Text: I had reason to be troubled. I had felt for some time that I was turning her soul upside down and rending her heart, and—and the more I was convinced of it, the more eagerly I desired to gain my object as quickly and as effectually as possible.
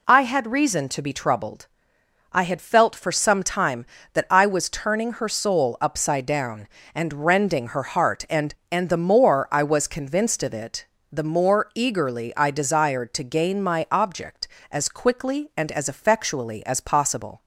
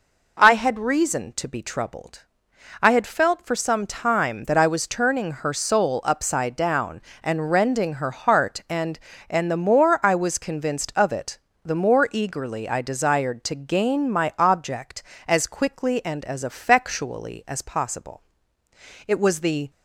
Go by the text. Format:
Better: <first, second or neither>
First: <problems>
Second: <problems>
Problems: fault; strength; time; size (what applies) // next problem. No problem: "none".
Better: first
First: none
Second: goes on to say "It was the"; noticeable; from 19.0 s on; 0.62 s long